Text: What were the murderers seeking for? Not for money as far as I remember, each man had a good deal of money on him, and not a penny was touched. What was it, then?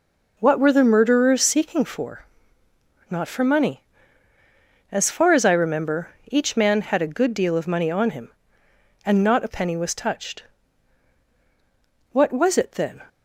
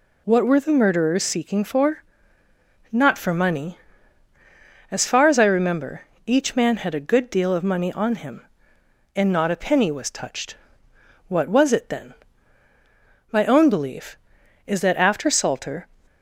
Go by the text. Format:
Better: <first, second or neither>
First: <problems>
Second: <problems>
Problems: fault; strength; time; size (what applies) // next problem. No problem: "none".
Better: first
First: none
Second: goes on to say "My own belief is that after Salter"; strong; from 13.3 s on; 2.5 s long